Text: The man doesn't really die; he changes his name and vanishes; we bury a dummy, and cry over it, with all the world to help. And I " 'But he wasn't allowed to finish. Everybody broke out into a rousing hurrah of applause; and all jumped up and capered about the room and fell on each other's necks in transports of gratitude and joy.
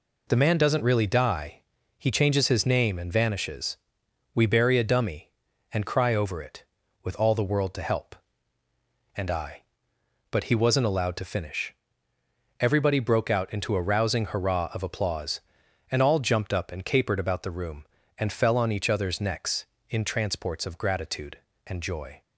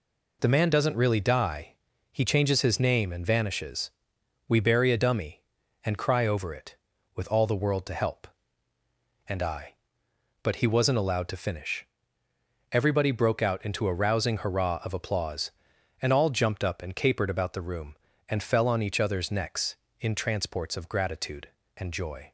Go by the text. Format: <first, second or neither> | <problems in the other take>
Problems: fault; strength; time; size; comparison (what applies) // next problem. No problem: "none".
neither | none